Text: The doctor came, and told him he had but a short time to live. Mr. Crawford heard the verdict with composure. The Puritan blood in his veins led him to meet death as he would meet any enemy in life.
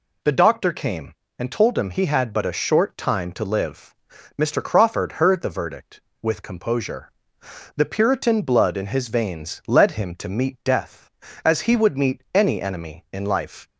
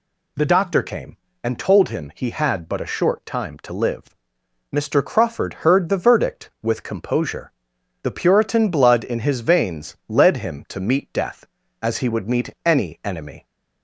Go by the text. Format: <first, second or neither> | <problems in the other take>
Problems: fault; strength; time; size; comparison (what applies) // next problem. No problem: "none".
first | pauses between "meet" and "any"; slight; at 12.4 s; 0.16 s long // stops before "in life"; at 13.4 s